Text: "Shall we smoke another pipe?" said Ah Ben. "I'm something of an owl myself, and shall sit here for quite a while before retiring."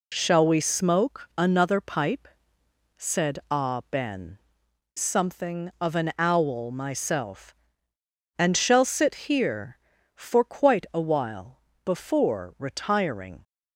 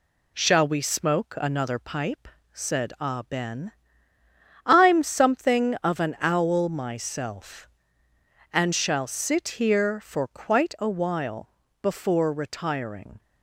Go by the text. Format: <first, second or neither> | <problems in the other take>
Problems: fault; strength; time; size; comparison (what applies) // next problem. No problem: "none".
second | skips "I'm"; at 4.6 s // pauses between "while" and "before"; slight; at 11.5 s; 0.24 s long; slight in the second